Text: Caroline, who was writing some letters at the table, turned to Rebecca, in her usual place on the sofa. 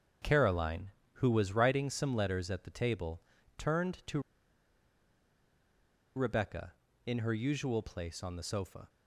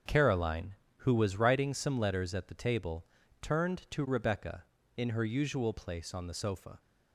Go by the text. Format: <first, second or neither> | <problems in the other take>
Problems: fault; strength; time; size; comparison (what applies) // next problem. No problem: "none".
second | starts louder than the rest; strong; until 1.4 s; 7.5 dB; strong in the second // pauses between "to" and "Rebecca"; strong; at 4.2 s; 1.9 s long